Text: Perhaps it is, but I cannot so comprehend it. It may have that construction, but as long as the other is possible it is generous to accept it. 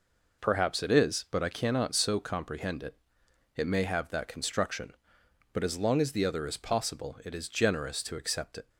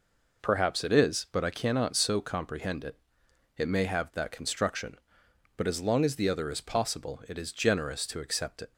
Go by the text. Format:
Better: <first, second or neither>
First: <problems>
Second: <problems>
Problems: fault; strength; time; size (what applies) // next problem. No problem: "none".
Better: neither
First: none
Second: none